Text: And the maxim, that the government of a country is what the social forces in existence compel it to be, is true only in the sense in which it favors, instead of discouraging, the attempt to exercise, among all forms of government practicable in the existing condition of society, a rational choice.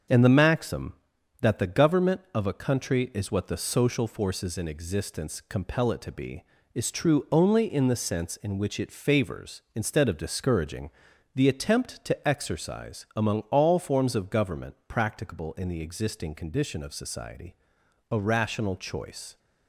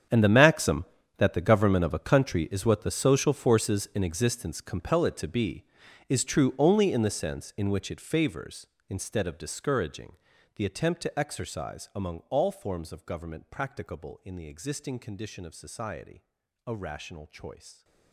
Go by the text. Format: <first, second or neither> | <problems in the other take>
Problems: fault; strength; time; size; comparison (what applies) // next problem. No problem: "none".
first | gets quieter; strong; throughout; 17 dB // starts louder than the rest; strong; until 1.4 s; 8 dB; strong in the first